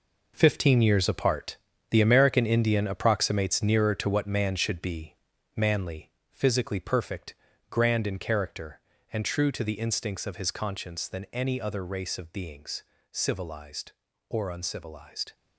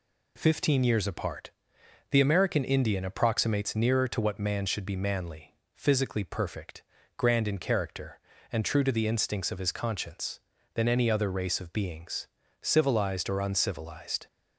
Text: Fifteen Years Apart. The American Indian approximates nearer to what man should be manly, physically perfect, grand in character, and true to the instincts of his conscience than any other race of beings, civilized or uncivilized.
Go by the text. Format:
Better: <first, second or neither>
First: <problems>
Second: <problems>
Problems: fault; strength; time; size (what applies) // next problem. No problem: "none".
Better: second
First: gets quieter; strong; throughout; 10.5 dB // pauses between "be" and "manly"; at 5.1 s; 0.40 s long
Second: none